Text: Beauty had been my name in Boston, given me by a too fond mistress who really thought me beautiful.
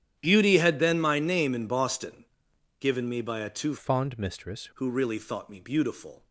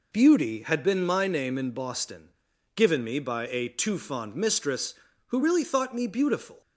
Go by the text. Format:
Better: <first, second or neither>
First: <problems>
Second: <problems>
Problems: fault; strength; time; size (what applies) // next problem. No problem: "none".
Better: second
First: starts louder than the rest; strong; until 1.2 s; 10 dB // changes voice from "fond" to "mistress"; from 3.7 to 4.6 s; 0.9 s long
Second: none